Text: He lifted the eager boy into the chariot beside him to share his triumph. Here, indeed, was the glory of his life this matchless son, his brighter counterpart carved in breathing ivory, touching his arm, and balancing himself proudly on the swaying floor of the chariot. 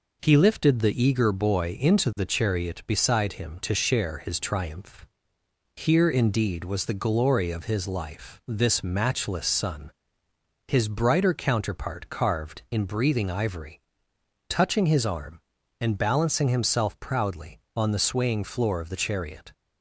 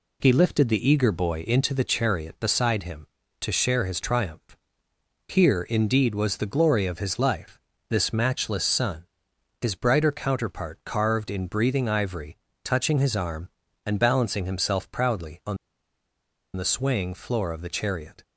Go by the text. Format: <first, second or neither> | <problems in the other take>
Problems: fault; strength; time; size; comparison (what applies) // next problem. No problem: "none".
first | pauses between "life" and "this"; slight; at 7.5 s; 0.32 s long // pauses between "on" and "the"; at 15.5 s; 0.99 s long